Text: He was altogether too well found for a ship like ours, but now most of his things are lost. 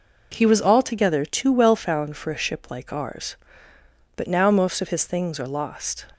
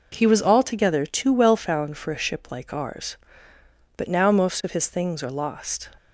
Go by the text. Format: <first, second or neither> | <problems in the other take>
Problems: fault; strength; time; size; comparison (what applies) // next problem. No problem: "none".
neither | none